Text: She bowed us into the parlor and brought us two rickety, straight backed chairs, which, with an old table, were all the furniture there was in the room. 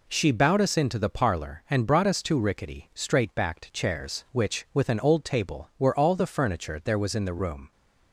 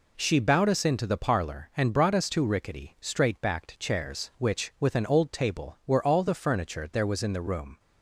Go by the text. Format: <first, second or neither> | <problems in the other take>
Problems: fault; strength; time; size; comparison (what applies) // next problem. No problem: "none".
neither | none